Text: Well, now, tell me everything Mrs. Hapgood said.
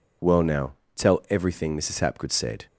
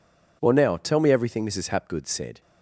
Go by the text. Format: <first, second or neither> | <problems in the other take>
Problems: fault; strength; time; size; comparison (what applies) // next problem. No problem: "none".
second | skips "me"; at 1.2 s